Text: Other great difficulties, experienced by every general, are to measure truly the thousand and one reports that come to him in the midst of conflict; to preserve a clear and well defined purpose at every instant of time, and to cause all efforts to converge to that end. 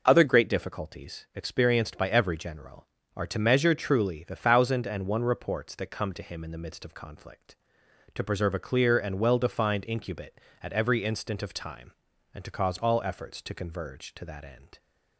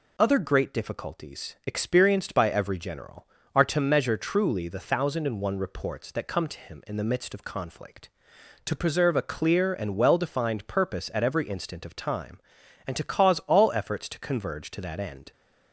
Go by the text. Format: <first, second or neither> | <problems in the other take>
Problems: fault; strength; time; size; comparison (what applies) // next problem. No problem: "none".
second | says "incubate" for "purpose"; at 9.8 s